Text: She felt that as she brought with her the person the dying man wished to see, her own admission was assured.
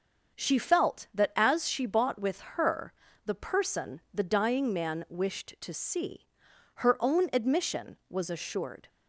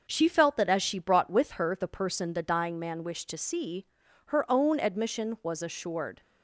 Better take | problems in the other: second | starts louder than the rest; until 1.4 s; 6.5 dB; noticeable in the second // says "bought" for "brought"; at 1.8 s // pauses between "her" and "the"; slight; at 2.9 s; 0.34 s long

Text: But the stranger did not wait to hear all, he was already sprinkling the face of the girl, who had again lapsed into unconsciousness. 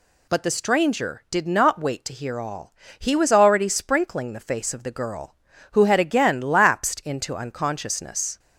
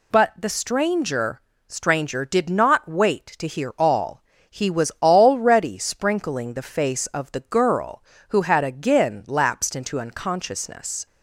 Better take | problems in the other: first | says "stranger" twice; at 1.6 s

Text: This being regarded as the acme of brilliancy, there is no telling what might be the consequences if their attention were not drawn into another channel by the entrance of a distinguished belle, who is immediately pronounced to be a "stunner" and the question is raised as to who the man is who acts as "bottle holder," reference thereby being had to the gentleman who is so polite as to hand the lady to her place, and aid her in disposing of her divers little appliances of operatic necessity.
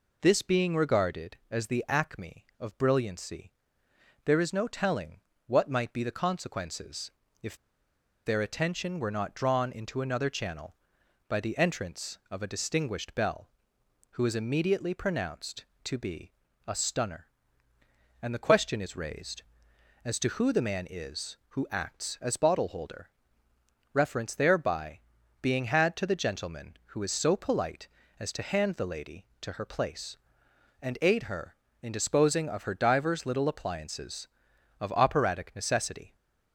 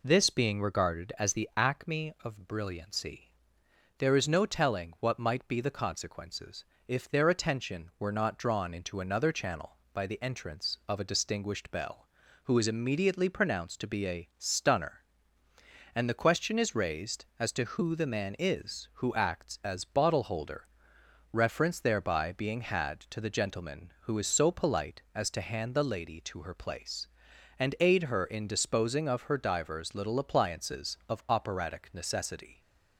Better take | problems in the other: second | pauses between "telling" and "what"; slight; at 5.1 s; 0.26 s long // pauses between "consequences" and "if"; slight; at 7.1 s; 0.30 s long; slight in the second // pauses between "if" and "their"; noticeable; at 7.5 s; 0.70 s long // pauses between "be" and "a"; slight; at 16.3 s; 0.34 s long // pauses between "thereby" and "being"; at 25.0 s; 0.40 s long

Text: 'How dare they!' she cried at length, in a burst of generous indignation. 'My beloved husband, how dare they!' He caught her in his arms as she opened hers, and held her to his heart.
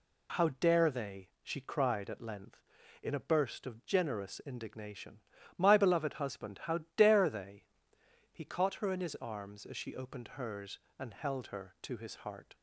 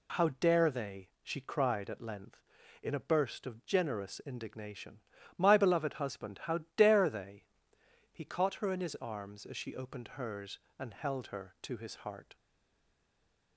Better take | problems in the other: first | stays silent after the last word; noticeable; from 12.3 s on; 1.2 s long

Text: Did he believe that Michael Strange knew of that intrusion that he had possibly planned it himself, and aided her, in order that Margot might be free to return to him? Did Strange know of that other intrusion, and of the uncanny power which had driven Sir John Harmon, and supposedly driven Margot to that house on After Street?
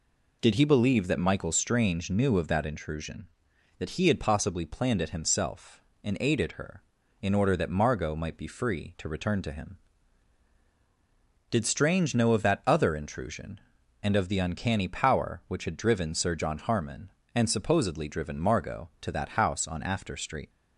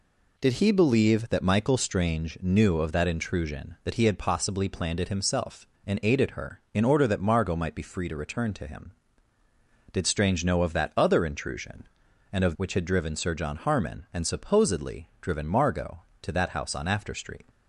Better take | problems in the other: first | skips "the uncanny power"; at 12.5 s

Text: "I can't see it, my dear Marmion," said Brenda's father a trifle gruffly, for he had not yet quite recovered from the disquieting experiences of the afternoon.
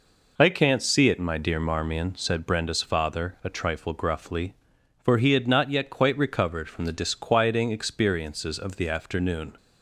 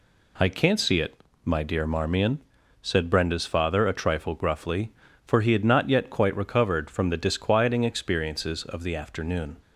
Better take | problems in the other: neither | none

